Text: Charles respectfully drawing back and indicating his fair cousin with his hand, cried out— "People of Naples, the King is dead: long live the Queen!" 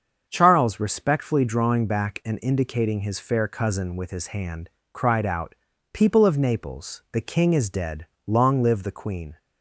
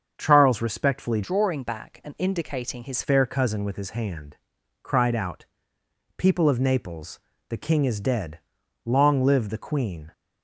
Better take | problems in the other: first | starts louder than the rest; until 1.1 s; 7 dB; also in the first // changes voice from "drawing" to "his"; from 1.2 to 3.0 s; 1.8 s long

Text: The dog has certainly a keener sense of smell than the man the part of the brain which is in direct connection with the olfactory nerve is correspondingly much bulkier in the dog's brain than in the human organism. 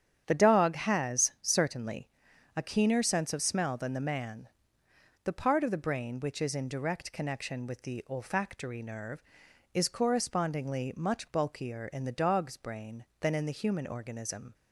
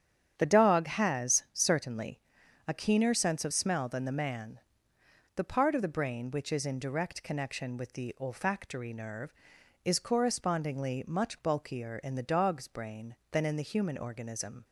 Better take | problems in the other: neither | starts louder than the rest; strong; the same in both // pauses between "certainly" and "a"; noticeable; the same in both // pauses between "man" and "the"; noticeable; the same in both

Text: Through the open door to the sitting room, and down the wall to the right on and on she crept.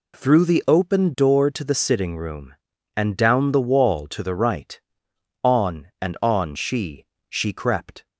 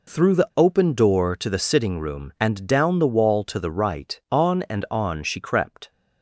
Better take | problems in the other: second | says "she" twice; at 7.2 s

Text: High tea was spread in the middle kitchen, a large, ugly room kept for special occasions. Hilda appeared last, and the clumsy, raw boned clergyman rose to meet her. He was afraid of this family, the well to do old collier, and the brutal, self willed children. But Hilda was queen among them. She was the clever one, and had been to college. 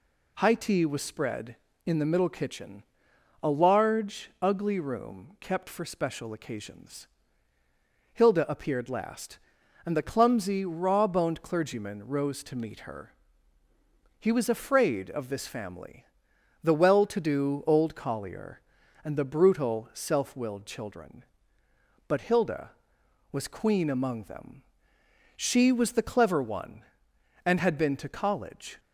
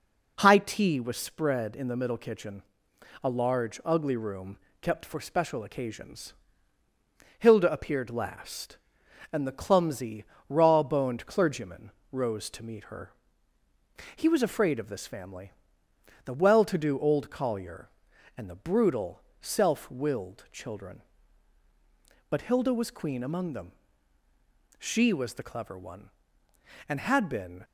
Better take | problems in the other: first | pauses between "room" and "kept"; slight; at 4.5 s; 0.24 s long // pauses between "clergyman" and "rose"; slight; at 11.9 s; 0.20 s long // stops before "to college"; at 27.6 s

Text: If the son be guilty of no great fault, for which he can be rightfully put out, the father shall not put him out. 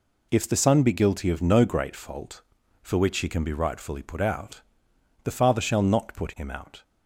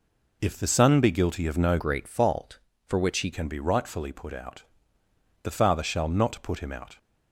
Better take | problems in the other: first | changes voice from "great" to "he"; from 1.7 to 3.3 s; 1.6 s long

